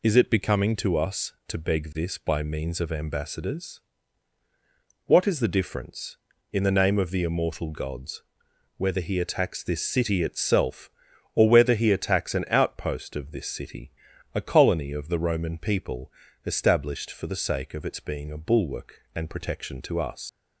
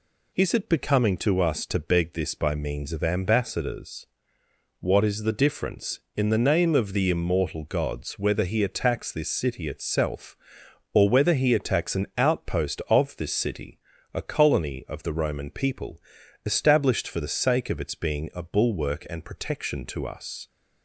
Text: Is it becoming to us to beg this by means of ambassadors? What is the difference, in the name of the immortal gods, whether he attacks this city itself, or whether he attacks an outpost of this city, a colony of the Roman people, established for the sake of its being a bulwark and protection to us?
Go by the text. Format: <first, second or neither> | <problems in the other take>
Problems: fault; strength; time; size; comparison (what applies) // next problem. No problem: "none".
second | leaves "us" unfinished; at 20.2 s; 100 ms